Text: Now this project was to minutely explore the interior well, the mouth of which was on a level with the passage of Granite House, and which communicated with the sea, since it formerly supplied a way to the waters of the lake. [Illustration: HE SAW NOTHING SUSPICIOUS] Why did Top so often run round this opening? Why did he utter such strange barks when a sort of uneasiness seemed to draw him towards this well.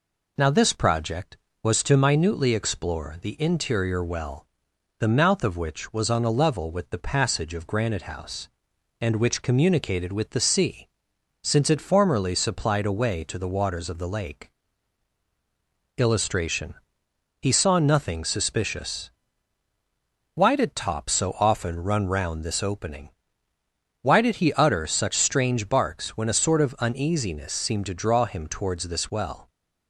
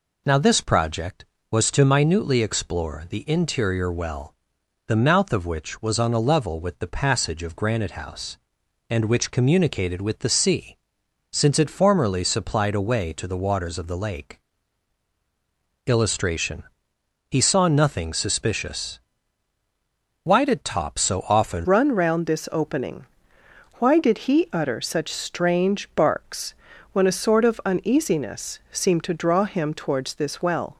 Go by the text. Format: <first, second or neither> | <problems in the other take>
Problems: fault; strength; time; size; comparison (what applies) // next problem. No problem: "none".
first | pauses between "SUSPICIOUS" and "Why"; at 18.9 s; 1.2 s long; also in the first // changes voice at "run"; from 21.6 s on; 9.1 s long // pauses between "barks" and "when"; at 26.5 s; 0.38 s long